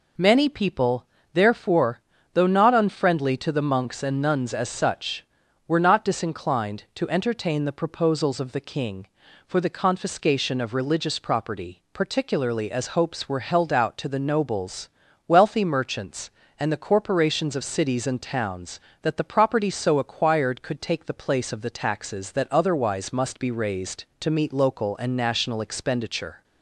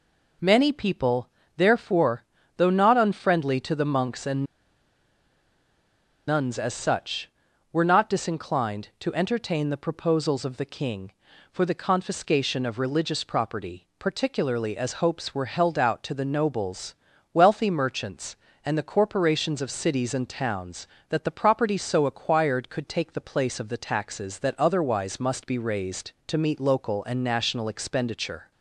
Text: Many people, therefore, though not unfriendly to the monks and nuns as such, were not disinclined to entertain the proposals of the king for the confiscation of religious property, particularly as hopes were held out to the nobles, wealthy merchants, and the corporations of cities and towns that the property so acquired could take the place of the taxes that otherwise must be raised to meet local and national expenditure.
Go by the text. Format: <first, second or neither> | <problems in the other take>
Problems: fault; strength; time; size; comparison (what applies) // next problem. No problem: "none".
first | pauses between "and" and "nuns"; strong; at 4.4 s; 1.8 s long